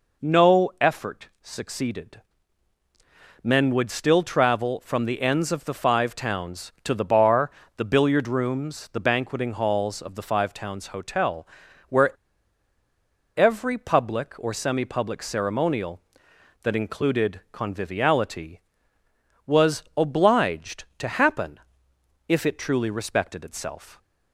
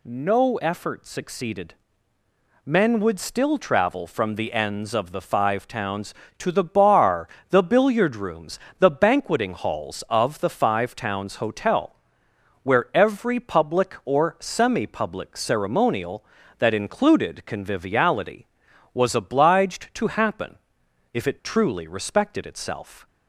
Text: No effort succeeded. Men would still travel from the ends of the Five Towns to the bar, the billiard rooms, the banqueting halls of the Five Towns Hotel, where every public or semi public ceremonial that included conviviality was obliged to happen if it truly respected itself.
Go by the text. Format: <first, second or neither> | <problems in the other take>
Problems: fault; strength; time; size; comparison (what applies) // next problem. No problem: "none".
second | pauses between "where" and "every"; strong; at 12.1 s; 1.2 s long // pauses between "happen" and "if"; noticeable; at 21.6 s; 0.66 s long; noticeable in the second